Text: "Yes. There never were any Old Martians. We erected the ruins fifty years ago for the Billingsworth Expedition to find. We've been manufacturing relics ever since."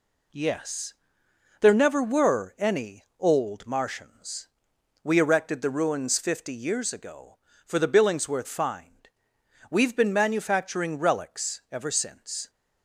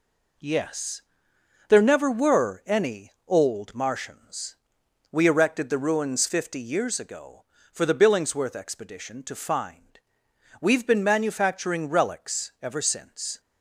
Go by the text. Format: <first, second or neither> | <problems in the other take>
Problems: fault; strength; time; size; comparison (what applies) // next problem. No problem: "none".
second | skips "Expedition to"; at 8.4 s